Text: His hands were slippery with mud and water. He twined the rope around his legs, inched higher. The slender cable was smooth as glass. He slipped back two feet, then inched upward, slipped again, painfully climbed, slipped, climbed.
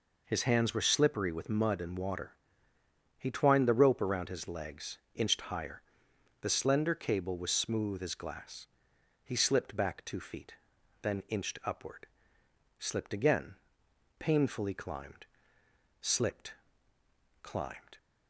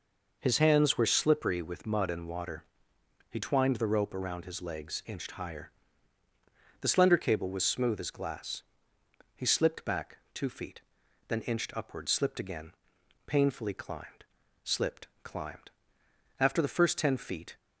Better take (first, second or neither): first